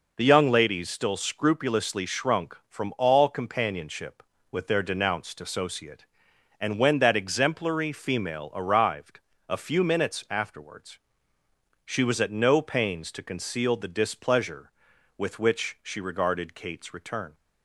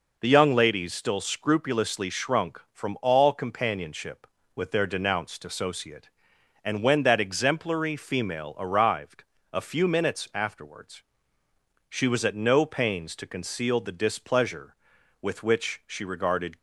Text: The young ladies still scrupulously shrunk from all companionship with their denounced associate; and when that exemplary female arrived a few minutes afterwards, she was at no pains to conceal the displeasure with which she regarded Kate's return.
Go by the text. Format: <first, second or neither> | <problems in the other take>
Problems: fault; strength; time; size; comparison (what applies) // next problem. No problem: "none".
first | pauses between "arrived" and "a"; slight; at 9.2 s; 0.30 s long; slight in the first // stops before "Kate's return"; at 16.5 s